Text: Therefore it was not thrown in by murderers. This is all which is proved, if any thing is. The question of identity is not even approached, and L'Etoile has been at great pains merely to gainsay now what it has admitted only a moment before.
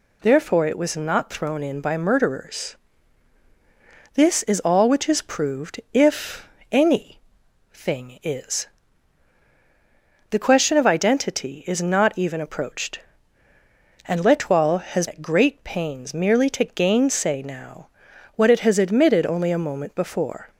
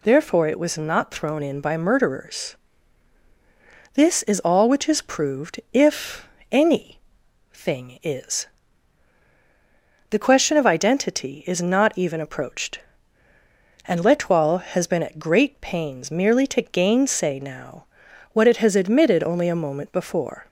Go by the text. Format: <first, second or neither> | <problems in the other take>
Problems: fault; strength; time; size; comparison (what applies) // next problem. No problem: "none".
second | pauses between "if" and "any"; slight; at 6.4 s; 0.24 s long; slight in the second // pauses between "any" and "thing"; noticeable; at 7.1 s; 0.52 s long; noticeable in the second // skips "been"; at 15.0 s // pauses between "now" and "what"; noticeable; at 17.8 s; 0.48 s long; noticeable in the second